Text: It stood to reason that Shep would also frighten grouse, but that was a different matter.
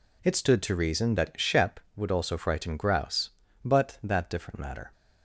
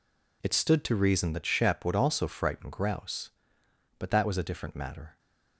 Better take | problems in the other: second | skips "was a"; at 4.2 s

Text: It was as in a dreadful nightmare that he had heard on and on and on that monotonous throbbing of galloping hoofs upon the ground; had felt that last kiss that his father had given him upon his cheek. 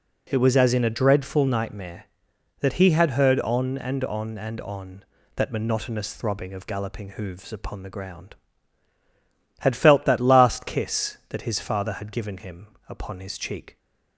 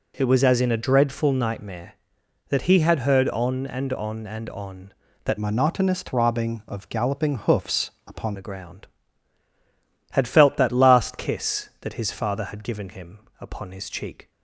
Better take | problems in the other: first | changes voice from "monotonous" to "upon"; from 5.3 to 8.3 s; 3.0 s long // pauses between "hoofs" and "upon"; slight; at 7.8 s; 0.16 s long // pauses between "him" and "upon"; slight; at 13.1 s; 0.22 s long; slight in the first

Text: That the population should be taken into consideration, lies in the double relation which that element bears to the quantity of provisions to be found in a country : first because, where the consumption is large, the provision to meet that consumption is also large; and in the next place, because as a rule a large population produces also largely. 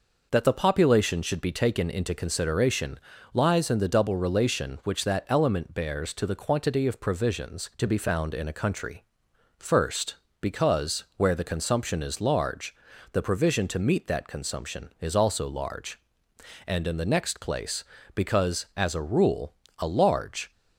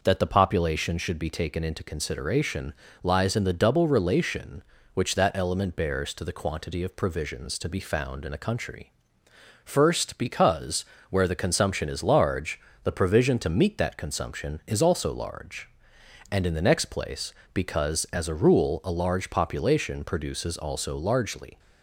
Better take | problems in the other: second | pauses between "rule" and "a"; slight; at 19.5 s; 0.26 s long // stops before "population produces also largely"; at 20.5 s

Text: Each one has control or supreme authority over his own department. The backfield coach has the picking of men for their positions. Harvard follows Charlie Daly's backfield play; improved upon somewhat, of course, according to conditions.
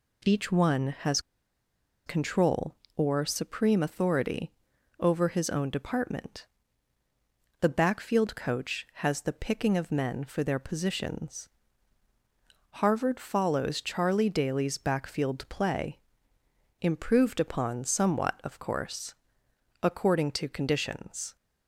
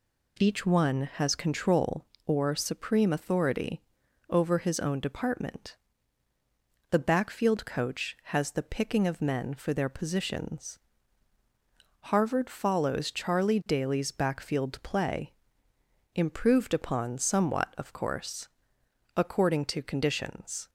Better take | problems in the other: second | pauses between "has" and "control"; noticeable; at 1.1 s; 0.87 s long // pauses between "authority" and "over"; noticeable; at 4.5 s; 0.48 s long; noticeable in the second

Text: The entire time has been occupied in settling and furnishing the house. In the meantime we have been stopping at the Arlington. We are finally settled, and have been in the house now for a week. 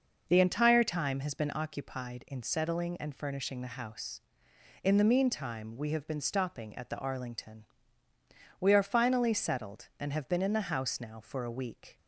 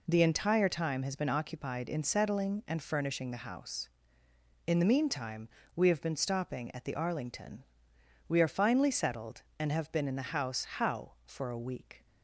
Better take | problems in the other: first | pauses between "meantime" and "we"; slight; at 5.4 s; 0.26 s long // says "how" for "now"; at 10.6 s

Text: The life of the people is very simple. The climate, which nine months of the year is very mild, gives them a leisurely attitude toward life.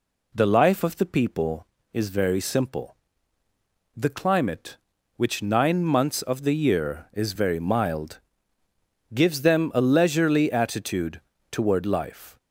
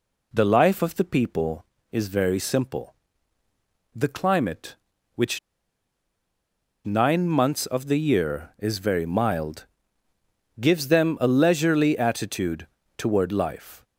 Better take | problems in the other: first | pauses between "which" and "nine"; strong; at 5.3 s; 1.4 s long // pauses between "attitude" and "toward"; slight; at 12.6 s; 0.32 s long; slight in the first

